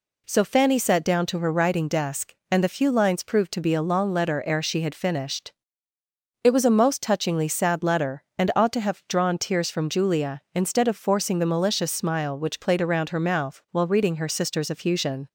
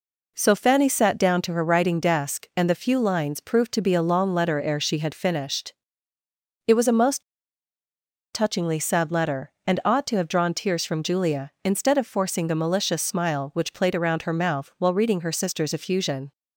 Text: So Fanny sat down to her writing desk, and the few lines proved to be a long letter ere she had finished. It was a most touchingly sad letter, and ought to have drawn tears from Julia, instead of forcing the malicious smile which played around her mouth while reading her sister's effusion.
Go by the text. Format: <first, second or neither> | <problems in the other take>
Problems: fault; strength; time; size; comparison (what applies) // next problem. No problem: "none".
first | pauses between "most" and "touchingly"; at 7.2 s; 1.1 s long